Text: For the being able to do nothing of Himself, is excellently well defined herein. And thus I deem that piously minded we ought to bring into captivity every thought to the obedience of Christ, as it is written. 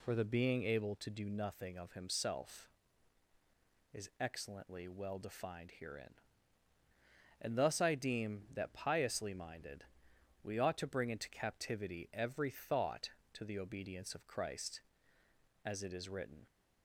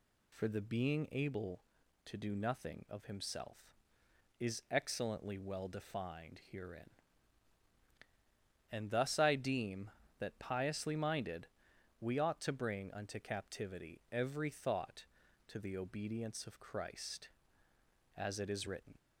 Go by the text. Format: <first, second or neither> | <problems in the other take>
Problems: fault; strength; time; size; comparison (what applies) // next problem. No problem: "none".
first | pauses between "minded" and "we"; noticeable; at 11.4 s; 0.54 s long; noticeable in the first // says "unto" for "into"; at 12.9 s